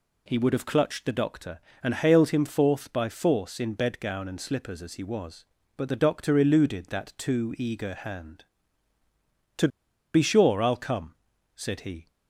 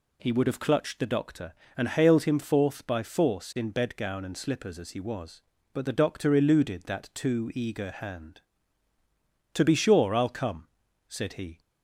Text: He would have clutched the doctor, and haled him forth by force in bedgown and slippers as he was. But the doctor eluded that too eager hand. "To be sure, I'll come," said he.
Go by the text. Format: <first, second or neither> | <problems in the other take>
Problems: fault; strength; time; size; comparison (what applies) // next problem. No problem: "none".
second | pauses between "To" and "be"; at 9.6 s; 0.45 s long